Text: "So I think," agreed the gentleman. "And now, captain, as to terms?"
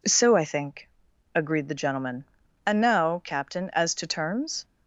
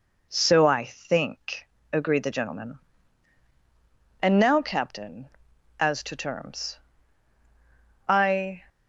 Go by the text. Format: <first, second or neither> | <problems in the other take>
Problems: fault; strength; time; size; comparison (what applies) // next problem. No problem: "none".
first | goes on to say "I"; from 8.0 s on; 0.56 s long